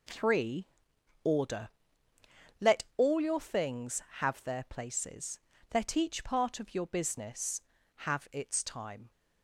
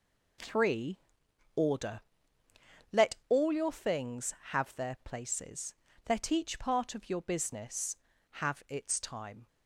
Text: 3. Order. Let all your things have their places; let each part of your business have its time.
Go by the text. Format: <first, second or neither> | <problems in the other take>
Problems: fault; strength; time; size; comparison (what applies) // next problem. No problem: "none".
neither | none